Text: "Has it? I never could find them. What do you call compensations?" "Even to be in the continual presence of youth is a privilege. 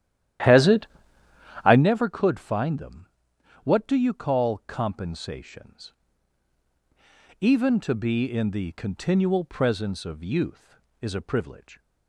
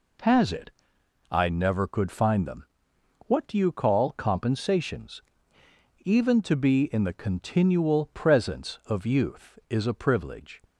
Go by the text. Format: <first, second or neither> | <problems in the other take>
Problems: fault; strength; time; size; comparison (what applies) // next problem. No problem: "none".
second | starts louder than the rest; strong; until 1.9 s; 12 dB